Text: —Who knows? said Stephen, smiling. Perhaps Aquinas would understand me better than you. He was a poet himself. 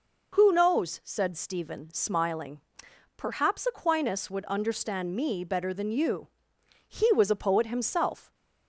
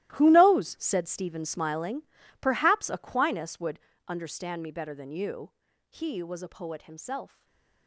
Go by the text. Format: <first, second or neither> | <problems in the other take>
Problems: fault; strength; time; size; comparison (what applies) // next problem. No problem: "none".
first | gets quieter; strong; throughout; 17 dB // pauses between "would" and "understand"; slight; at 3.7 s; 0.28 s long // stays silent after the last word; slight; from 7.2 s on; 0.6 s long